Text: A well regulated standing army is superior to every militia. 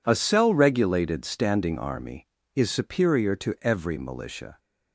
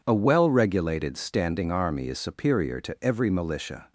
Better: second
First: says "cell" for "well"; at 0.1 s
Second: none

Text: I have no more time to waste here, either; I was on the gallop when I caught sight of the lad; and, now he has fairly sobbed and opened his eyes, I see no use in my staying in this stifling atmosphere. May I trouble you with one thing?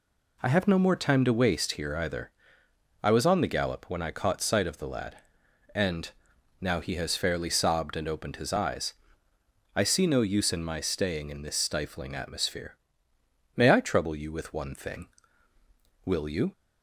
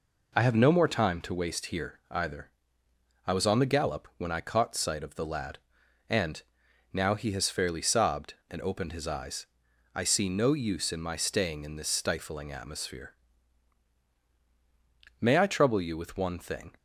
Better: second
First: goes on to say "Will you"; slight; from 16.0 s on; 0.46 s long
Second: none

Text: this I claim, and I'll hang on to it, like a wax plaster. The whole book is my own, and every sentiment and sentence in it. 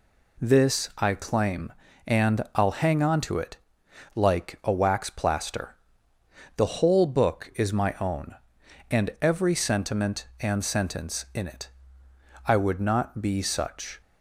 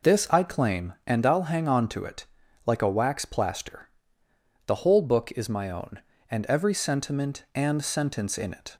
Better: second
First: goes on to say "I would not be such"; from 12.4 s on; 1.5 s long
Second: none

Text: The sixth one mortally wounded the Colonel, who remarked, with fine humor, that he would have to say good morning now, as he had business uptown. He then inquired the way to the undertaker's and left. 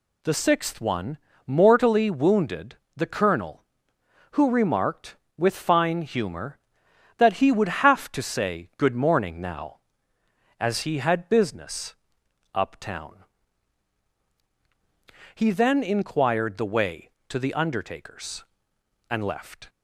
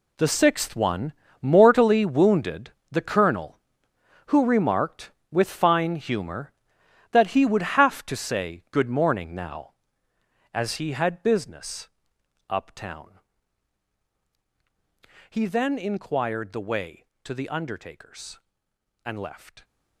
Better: first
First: pauses between "one" and "mortally"; slight; at 1.1 s; 0.28 s long // pauses between "wounded" and "the"; slight; at 2.7 s; 0.22 s long // pauses between "business" and "uptown"; noticeable; at 11.9 s; 0.60 s long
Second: gets quieter; strong; throughout; 13.5 dB // pauses between "one" and "mortally"; slight; at 1.1 s; 0.28 s long // pauses between "wounded" and "the"; slight; at 2.6 s; 0.22 s long // pauses between "business" and "uptown"; noticeable; at 11.8 s; 0.62 s long

